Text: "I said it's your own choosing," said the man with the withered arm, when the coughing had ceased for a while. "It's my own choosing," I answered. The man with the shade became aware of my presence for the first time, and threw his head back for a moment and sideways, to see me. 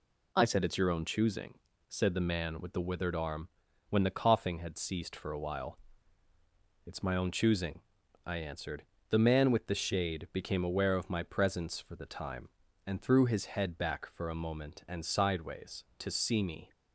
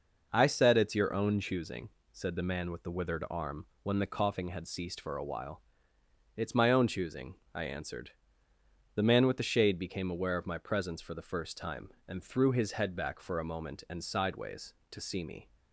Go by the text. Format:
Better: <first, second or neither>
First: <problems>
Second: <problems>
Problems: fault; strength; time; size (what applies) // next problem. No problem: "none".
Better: second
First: skips "first"; at 12.0 s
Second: none